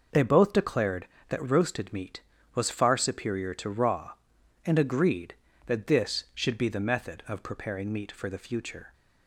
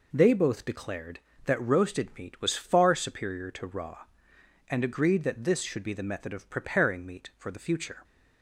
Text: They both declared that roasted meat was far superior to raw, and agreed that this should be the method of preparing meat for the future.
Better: neither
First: none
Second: none

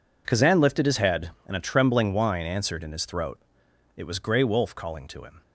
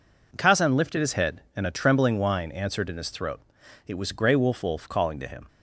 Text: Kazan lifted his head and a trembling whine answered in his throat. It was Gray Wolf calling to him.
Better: first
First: none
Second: says "Wolf" twice; at 4.6 s

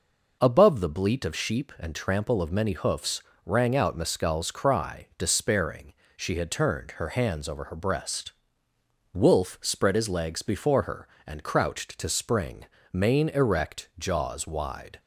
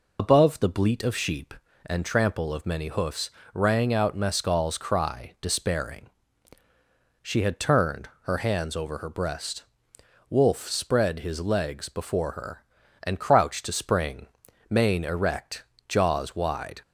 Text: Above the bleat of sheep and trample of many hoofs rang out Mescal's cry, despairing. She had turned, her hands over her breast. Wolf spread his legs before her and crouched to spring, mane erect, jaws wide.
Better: first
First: pauses between "hoofs" and "rang"; slight; at 3.2 s; 0.24 s long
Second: loses the start of "Above"; at 0.1 s; 85 ms // pauses between "hoofs" and "rang"; slight; at 3.3 s; 0.24 s long

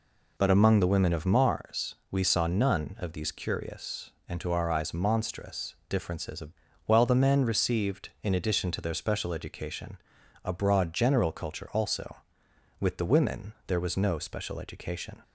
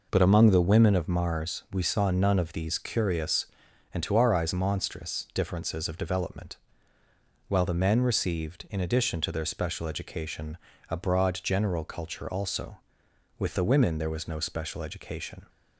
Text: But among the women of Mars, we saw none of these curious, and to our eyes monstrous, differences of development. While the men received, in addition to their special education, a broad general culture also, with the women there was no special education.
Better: second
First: skips "development"; at 6.6 s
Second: none

